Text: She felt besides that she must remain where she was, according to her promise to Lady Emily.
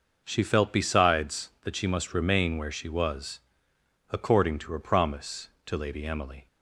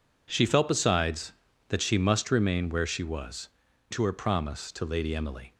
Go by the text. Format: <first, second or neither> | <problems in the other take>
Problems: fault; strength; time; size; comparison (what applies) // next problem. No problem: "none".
first | skips "according"; at 3.6 s